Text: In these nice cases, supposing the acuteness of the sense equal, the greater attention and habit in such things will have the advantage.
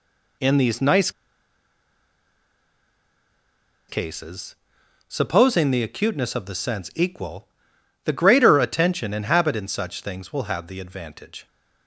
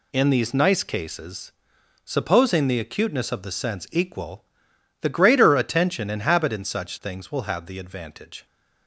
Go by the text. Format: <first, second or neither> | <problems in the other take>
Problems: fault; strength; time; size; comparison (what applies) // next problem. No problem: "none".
second | pauses between "nice" and "cases"; strong; at 1.1 s; 2.7 s long